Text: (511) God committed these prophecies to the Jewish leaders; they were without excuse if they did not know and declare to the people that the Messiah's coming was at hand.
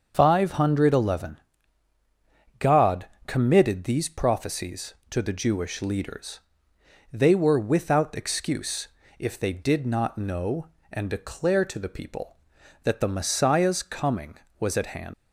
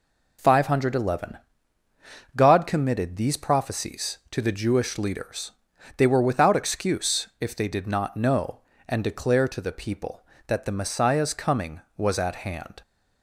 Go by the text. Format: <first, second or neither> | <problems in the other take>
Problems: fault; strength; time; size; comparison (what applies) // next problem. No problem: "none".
second | pauses between "God" and "committed"; slight; at 3.0 s; 0.20 s long // pauses between "excuse" and "if"; slight; at 8.8 s; 0.32 s long // leaves "hand" unfinished; at 15.1 s; 120 ms